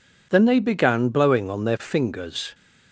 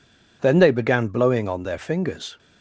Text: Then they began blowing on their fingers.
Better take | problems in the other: neither | none

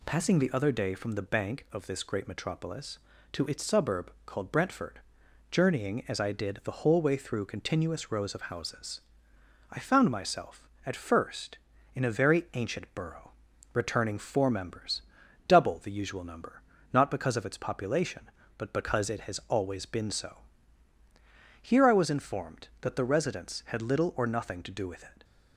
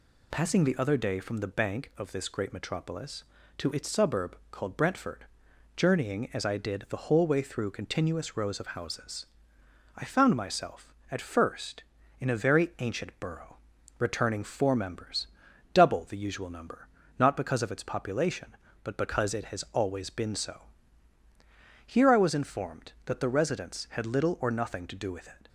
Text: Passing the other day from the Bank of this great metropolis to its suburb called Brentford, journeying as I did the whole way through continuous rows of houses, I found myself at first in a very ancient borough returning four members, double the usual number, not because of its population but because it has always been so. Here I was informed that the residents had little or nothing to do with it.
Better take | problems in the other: first | loses the start of "Passing"; at 0.3 s; 30 ms // pauses between "borough" and "returning"; at 13.5 s; 0.44 s long; also in the first

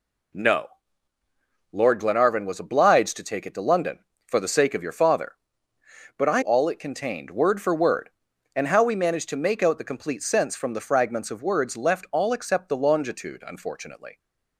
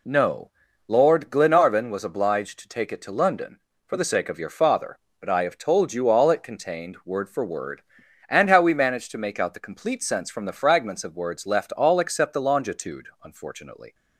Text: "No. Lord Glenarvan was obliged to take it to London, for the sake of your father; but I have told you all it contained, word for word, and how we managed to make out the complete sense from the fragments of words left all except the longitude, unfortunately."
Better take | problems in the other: second | skips "have told you"; at 6.4 s

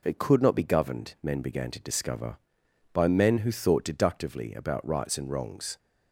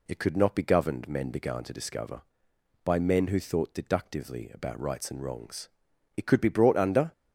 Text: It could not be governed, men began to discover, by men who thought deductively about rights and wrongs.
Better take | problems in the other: first | goes on to say "It could be brought under"; noticeable; from 6.1 s on; 0.96 s long

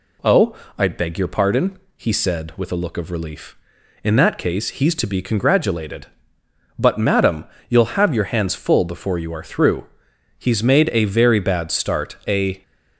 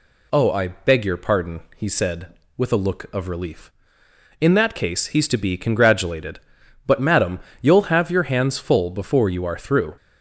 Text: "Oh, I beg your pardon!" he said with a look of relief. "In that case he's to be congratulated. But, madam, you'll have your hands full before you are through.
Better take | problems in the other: second | goes on to say "He's made a very bad start a"; strong; from 10.3 s on; 2.2 s long

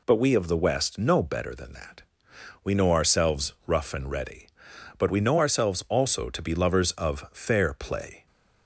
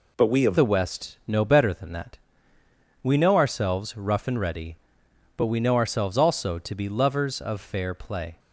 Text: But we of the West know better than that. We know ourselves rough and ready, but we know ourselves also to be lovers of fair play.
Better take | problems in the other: first | changes voice at "the"; from 0.5 s on; 7.8 s long

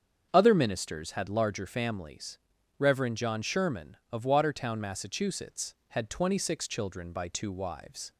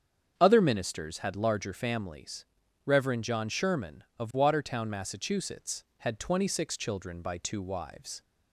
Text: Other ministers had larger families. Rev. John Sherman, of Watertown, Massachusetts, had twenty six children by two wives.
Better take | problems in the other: neither | starts louder than the rest; strong; the same in both

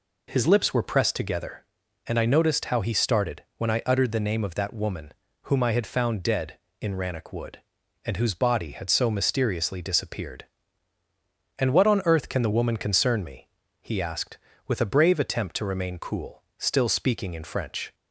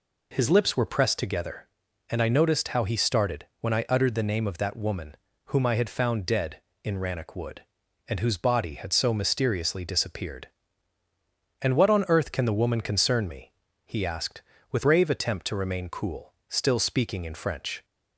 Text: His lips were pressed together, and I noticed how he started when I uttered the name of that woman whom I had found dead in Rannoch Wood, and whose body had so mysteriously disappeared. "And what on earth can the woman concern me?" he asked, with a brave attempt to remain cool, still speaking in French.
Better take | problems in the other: first | pauses between "started" and "when"; slight; at 3.4 s; 0.16 s long; slight in the first // pauses between "woman" and "whom"; slight; at 5.1 s; 0.32 s long; slight in the first // skips "a"; at 14.8 s

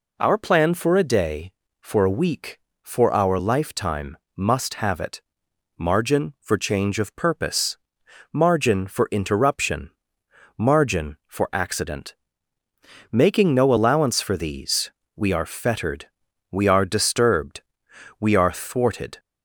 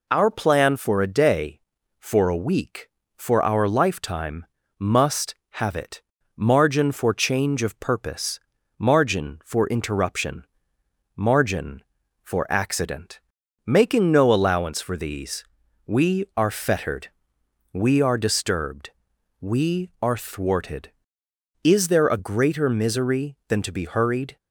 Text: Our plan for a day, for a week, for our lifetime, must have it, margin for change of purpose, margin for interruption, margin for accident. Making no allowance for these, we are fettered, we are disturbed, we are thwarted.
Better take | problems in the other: first | goes on to say "Is there a greater misery than to be hurried"; strong; from 21.6 s on; 2.7 s long

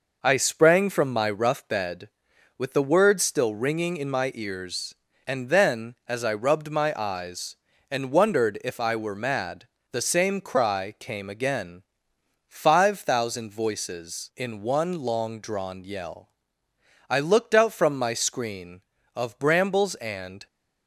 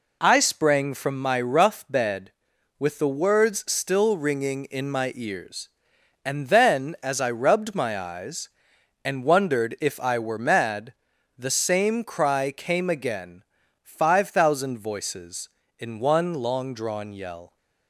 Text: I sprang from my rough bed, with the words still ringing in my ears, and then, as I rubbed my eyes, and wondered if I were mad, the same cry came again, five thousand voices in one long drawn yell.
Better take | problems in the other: second | goes on to say "I looked out from my screen of brambles and"; strong; from 17.0 s on; 3.3 s long

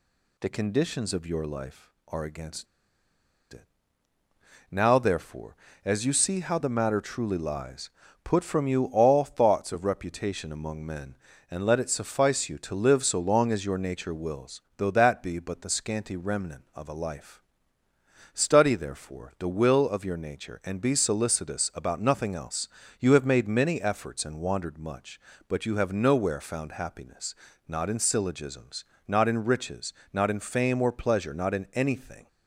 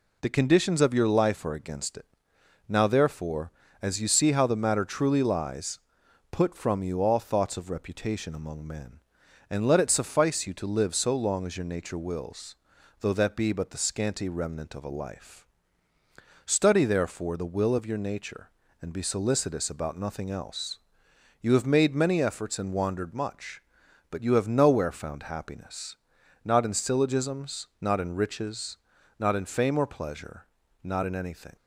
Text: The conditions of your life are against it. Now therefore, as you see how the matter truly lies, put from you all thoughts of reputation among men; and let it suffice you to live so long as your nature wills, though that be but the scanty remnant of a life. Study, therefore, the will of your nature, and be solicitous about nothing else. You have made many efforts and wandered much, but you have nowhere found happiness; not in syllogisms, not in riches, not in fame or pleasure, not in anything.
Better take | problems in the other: second | pauses between "against" and "it"; noticeable; at 2.6 s; 0.87 s long

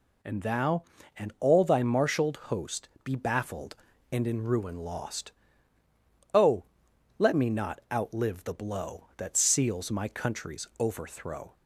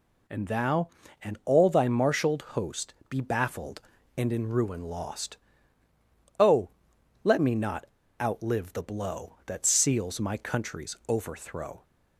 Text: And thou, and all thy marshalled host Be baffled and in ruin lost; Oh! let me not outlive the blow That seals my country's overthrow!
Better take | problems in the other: first | pauses between "host" and "Be"; slight; at 2.9 s; 0.16 s long; slight in the first // pauses between "not" and "outlive"; slight; at 7.8 s; 0.35 s long

